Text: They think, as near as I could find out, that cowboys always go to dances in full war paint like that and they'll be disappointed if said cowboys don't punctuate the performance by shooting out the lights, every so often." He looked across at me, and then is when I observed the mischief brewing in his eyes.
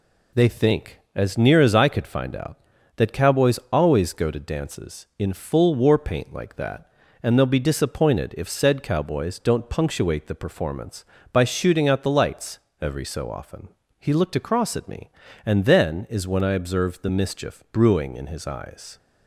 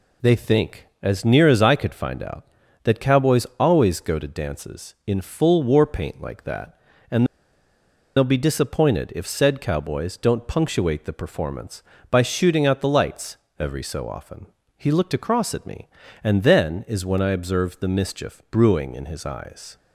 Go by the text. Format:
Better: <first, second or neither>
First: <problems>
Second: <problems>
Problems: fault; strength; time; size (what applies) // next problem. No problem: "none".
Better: first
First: none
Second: pauses between "and" and "they'll"; noticeable; at 7.2 s; 0.90 s long